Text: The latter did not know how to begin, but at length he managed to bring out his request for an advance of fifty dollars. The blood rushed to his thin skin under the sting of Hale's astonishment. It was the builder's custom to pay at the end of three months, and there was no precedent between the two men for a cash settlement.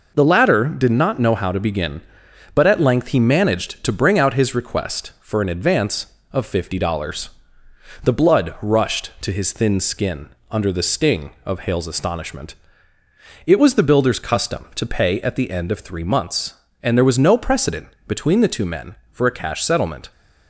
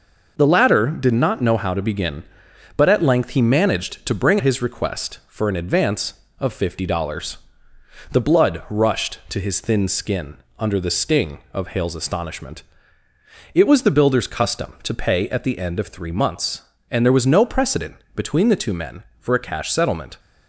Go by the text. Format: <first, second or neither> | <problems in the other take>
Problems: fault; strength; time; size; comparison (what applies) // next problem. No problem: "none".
first | skips "out"; at 4.4 s // pauses between "skin" and "under"; slight; at 10.3 s; 0.22 s long; slight in the first // pauses between "precedent" and "between"; slight; at 17.9 s; 0.18 s long; slight in the first